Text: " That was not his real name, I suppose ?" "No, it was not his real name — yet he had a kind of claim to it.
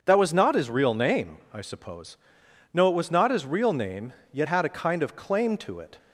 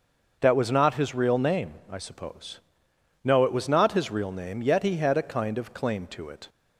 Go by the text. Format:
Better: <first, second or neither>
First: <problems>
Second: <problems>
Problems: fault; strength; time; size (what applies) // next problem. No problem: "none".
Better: second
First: starts louder than the rest; noticeable; until 1.0 s; 6 dB // skips "he"; at 4.4 s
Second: starts louder than the rest; until 1.3 s; 6.5 dB